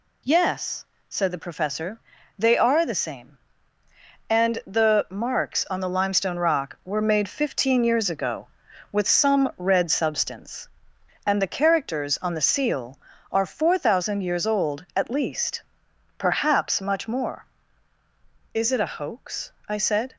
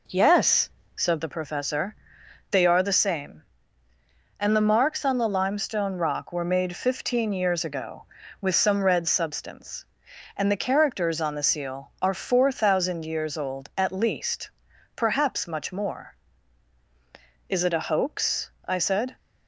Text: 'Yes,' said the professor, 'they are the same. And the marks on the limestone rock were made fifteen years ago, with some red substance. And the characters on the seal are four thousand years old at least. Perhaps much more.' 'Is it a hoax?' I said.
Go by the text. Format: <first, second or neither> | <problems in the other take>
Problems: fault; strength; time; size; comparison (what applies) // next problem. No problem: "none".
first | starts louder than the rest; noticeable; until 1.4 s; 4.5 dB